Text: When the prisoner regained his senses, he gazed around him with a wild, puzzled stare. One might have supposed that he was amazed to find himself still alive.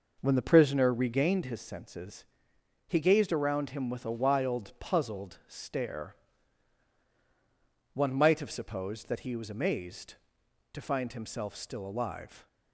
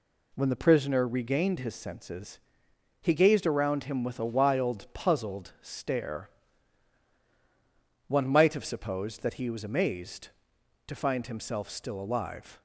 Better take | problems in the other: second | starts louder than the rest; noticeable; until 1.5 s; 5.5 dB

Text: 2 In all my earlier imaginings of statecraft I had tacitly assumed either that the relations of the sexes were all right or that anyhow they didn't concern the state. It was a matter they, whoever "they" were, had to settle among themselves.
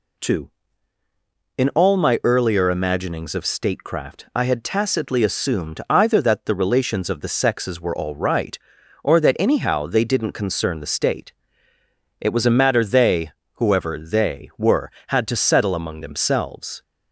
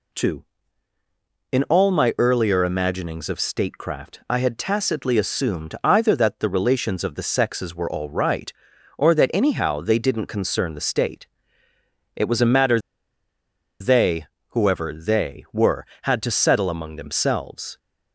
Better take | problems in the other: first | pauses between "matter" and "they"; at 12.7 s; 1.0 s long

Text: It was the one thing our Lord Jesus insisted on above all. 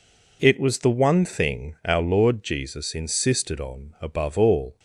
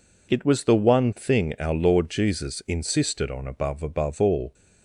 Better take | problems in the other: first | says "above" twice; at 3.8 s

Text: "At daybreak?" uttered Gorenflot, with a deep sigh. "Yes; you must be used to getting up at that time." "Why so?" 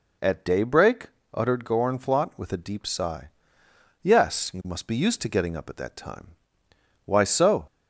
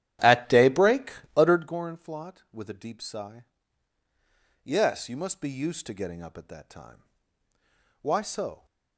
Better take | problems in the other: first | starts louder than the rest; strong; until 1.8 s; 12 dB

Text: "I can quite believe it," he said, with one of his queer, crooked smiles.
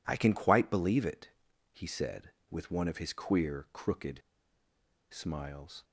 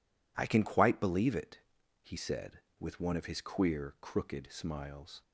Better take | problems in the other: second | pauses between "crooked" and "smiles"; noticeable; at 4.1 s; 0.91 s long

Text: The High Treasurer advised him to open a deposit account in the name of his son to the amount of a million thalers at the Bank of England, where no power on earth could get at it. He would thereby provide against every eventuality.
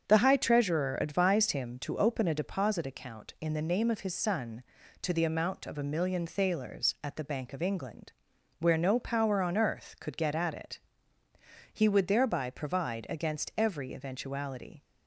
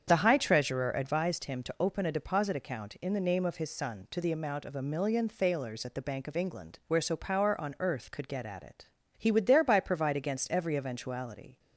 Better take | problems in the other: first | starts louder than the rest; strong; until 1.1 s; 7.5 dB; strong in the first // says "so" for "no"; at 7.0 s

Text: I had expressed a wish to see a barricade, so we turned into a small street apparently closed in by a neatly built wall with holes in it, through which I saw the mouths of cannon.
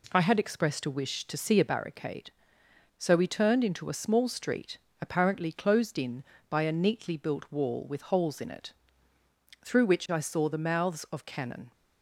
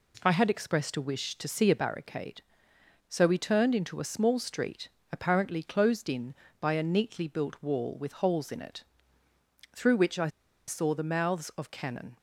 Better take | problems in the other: first | pauses between "street" and "apparently"; slight; at 4.8 s; 0.24 s long; slight in the first // pauses between "I" and "saw"; at 10.2 s; 0.38 s long

